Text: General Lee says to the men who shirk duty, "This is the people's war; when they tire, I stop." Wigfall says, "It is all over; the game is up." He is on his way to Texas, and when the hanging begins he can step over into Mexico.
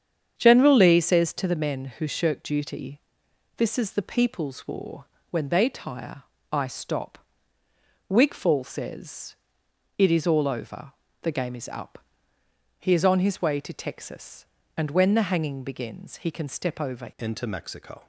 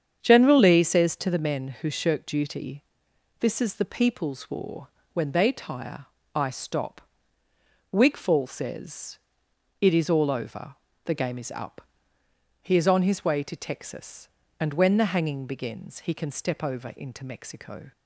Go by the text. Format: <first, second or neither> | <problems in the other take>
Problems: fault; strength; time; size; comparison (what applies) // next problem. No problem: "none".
second | starts louder than the rest; strong; until 1.3 s; 8 dB; strong in the second // changes voice at "into"; from 17.1 s on; 0.9 s long